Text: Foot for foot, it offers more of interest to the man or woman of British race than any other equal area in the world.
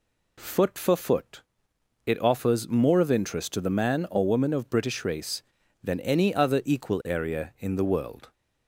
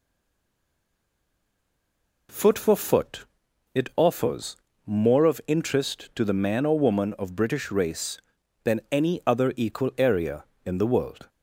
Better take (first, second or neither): first